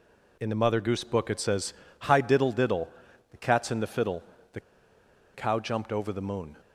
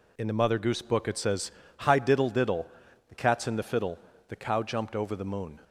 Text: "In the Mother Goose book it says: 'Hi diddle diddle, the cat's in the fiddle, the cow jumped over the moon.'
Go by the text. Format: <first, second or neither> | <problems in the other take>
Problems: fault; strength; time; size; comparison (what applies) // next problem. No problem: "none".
second | pauses between "the" and "cow"; noticeable; at 4.5 s; 0.74 s long